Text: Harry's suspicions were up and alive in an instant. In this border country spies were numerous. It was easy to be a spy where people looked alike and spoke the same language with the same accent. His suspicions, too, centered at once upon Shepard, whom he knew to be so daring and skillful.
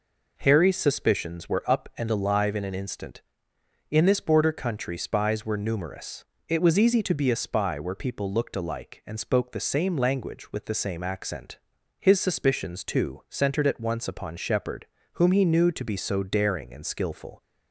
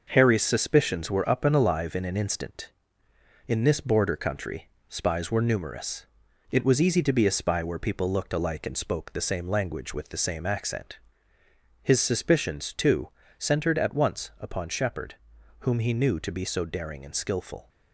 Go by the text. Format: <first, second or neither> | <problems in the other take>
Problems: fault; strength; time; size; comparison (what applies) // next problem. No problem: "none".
first | gets quieter; noticeable; throughout; 5.5 dB // pauses between "country" and "spies"; slight; at 4.6 s; 0.20 s long